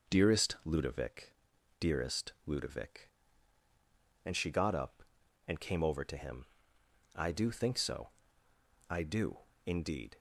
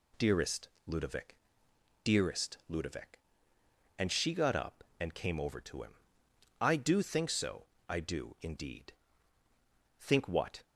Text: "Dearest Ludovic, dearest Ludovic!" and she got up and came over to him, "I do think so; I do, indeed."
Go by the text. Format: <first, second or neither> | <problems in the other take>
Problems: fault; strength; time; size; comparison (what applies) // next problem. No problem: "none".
first | pauses between "Dearest" and "Ludovic"; slight; at 0.6 s; 0.18 s long // goes on to say "Think what"; noticeable; from 9.9 s on; 0.64 s long